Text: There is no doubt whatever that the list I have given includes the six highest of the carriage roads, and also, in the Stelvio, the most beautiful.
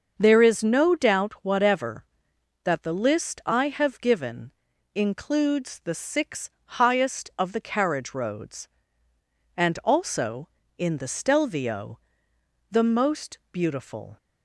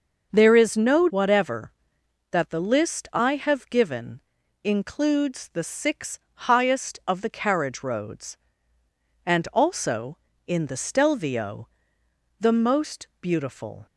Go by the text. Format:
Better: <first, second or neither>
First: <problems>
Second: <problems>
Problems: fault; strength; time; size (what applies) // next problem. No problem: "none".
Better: first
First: starts louder than the rest; until 1.1 s; 6.5 dB // pauses between "given" and "includes"; at 4.5 s; 0.42 s long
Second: starts louder than the rest; until 1.3 s; 6.5 dB // skips "doubt"; at 1.0 s // pauses between "given" and "includes"; at 4.1 s; 0.42 s long